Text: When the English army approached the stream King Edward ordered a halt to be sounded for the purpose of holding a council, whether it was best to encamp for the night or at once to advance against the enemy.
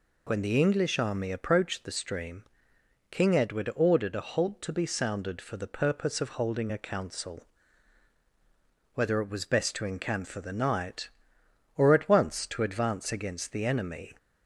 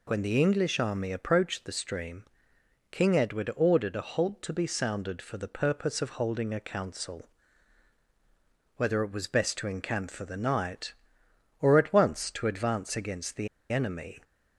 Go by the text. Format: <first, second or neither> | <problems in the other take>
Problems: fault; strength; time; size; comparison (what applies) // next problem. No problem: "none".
first | pauses between "stream" and "King"; noticeable; at 2.2 s; 0.66 s long; noticeable in the first // pauses between "the" and "enemy"; slight; at 13.4 s; 0.24 s long